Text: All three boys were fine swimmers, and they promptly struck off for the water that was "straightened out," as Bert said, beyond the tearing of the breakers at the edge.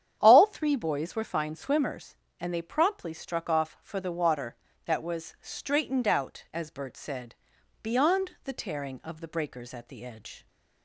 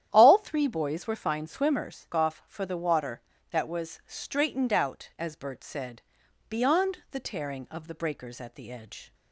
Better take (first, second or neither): first